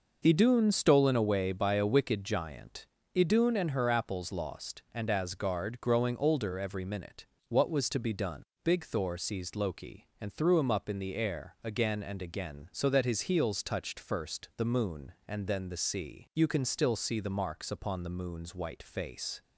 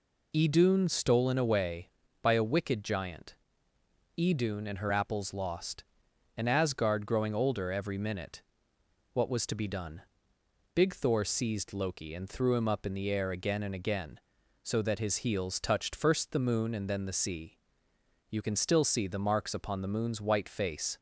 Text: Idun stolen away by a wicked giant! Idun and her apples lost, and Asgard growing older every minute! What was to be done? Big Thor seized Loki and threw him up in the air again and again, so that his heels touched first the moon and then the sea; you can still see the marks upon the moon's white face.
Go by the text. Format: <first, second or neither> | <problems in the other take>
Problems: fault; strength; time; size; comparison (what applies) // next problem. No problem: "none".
neither | none